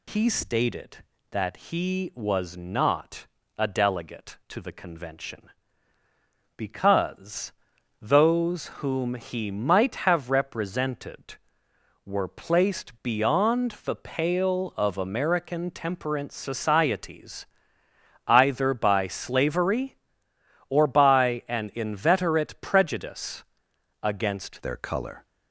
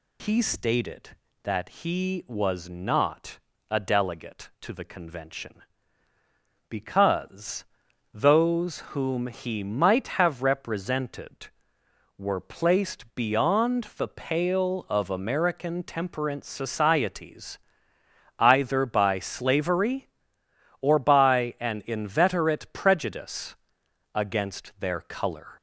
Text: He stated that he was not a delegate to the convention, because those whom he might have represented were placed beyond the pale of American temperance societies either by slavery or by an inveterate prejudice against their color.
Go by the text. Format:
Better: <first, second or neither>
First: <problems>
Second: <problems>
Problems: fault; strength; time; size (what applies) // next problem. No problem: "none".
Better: second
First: pauses between "not" and "a"; slight; at 3.2 s; 0.32 s long // pauses between "because" and "those"; noticeable; at 7.5 s; 0.48 s long // pauses between "societies" and "either"; noticeable; at 17.4 s; 0.82 s long // pauses between "prejudice" and "against"; noticeable; at 23.4 s; 0.60 s long // changes voice at "their"; from 24.6 s on; 0.6 s long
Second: pauses between "not" and "a"; slight; at 3.3 s; 0.32 s long // pauses between "because" and "those"; noticeable; at 7.6 s; 0.48 s long // pauses between "societies" and "either"; noticeable; at 17.5 s; 0.81 s long // pauses between "prejudice" and "against"; noticeable; at 23.5 s; 0.60 s long